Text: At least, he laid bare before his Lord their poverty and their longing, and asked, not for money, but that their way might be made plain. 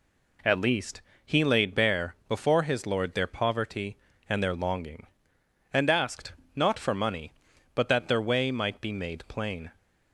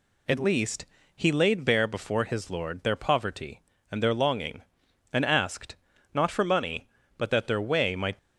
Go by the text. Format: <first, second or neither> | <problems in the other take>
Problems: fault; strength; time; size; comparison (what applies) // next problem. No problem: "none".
first | stops before "be made plain"; at 8.1 s